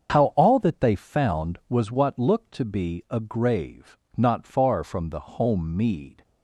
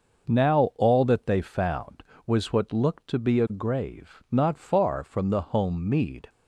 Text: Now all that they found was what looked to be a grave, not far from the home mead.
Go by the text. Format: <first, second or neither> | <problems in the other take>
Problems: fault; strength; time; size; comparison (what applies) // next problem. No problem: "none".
second | starts louder than the rest; until 1.1 s; 7 dB // says "How" for "Now"; at 0.1 s